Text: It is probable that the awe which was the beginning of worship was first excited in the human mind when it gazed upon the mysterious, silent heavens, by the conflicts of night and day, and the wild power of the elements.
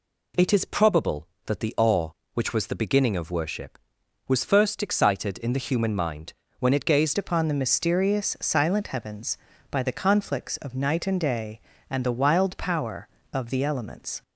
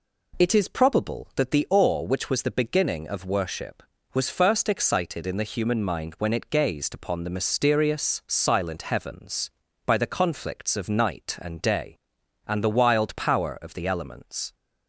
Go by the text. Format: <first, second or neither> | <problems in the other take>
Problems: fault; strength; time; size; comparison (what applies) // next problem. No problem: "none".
second | pauses between "mind" and "when"; slight; at 6.3 s; 0.26 s long // changes voice at "upon"; from 7.1 s on; 7.1 s long